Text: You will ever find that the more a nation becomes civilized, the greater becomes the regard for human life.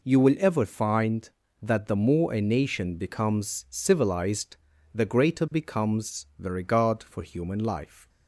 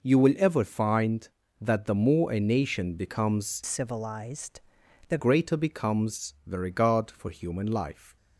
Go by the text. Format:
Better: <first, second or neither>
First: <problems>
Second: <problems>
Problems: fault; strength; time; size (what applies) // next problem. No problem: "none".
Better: first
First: none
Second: changes voice from "civilized" to "the"; from 3.6 to 5.1 s; 1.5 s long